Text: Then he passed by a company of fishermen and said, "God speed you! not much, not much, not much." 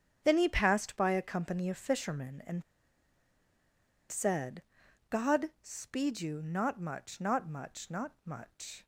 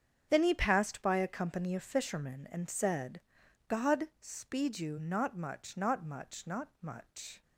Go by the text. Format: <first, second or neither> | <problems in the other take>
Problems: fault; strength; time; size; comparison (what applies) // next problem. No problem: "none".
second | starts louder than the rest; strong; until 1.2 s; 7.5 dB; strong in the second // pauses between "and" and "said"; strong; at 2.6 s; 1.4 s long